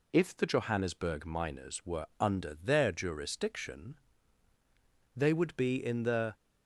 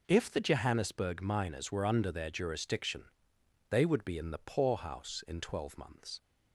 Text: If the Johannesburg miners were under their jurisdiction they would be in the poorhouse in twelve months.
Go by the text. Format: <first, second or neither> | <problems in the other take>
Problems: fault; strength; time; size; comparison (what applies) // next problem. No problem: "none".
second | pauses between "jurisdiction" and "they"; at 3.9 s; 1.1 s long; noticeable in the second // stops before "poorhouse in twelve months"; at 6.3 s